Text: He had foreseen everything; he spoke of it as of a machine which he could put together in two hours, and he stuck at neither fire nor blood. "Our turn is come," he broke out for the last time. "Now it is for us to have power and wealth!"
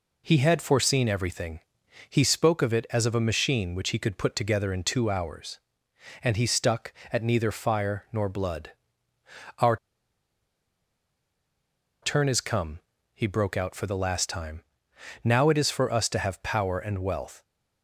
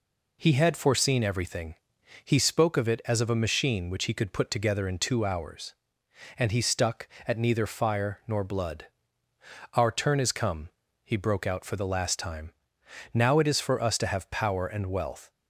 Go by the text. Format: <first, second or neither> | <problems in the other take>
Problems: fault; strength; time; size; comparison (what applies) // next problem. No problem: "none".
second | pauses between "Our" and "turn"; strong; at 9.7 s; 2.2 s long